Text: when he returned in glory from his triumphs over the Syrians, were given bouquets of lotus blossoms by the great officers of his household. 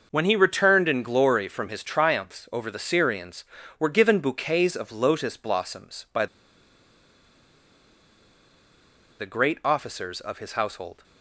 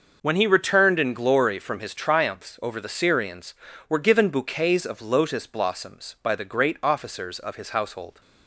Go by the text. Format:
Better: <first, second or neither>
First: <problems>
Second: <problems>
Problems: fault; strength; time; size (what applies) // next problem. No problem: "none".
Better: second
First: pauses between "by" and "the"; strong; at 6.2 s; 2.9 s long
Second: none